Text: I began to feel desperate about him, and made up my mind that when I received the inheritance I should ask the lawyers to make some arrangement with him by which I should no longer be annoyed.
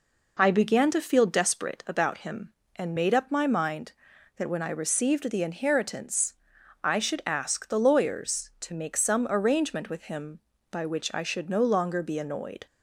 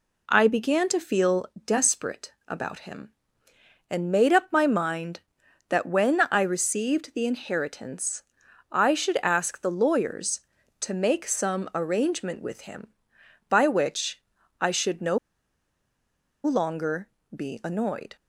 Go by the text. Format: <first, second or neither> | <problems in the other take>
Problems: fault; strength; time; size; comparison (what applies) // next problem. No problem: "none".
first | pauses between "feel" and "desperate"; slight; at 1.4 s; 0.20 s long // pauses between "desperate" and "about"; slight; at 2.3 s; 0.16 s long // pauses between "inheritance" and "I"; noticeable; at 8.2 s; 0.50 s long; noticeable in the first // pauses between "which" and "I"; at 14.2 s; 0.38 s long // pauses between "no" and "longer"; strong; at 15.1 s; 1.2 s long // pauses between "longer" and "be"; slight; at 17.0 s; 0.28 s long